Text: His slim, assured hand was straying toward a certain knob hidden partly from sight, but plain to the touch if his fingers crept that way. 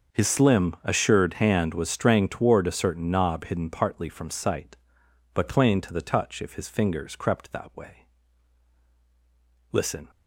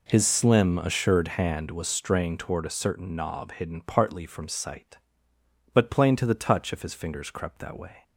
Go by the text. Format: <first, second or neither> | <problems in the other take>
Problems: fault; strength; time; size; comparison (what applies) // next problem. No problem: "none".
second | starts louder than the rest; until 1.2 s; 6.5 dB // goes on to say "Listen"; slight; from 9.7 s on; 0.40 s long